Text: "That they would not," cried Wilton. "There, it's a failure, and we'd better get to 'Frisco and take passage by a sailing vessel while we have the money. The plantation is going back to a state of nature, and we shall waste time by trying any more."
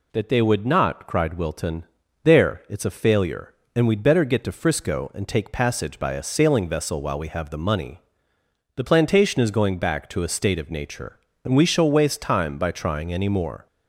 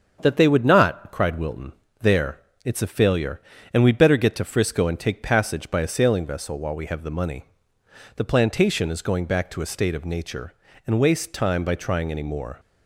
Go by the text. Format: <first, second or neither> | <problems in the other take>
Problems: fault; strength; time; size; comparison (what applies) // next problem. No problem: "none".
first | starts louder than the rest; until 1.2 s; 7 dB // skips "we shall"; at 10.9 s